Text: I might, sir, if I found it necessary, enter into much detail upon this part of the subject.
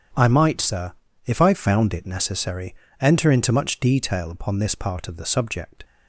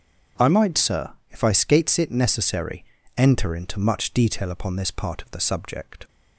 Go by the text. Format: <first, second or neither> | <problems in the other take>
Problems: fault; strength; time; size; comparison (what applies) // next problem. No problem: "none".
first | starts louder than the rest; strong; until 1.5 s; 7 dB; strong in the first // says "skates" for "found"; at 1.5 s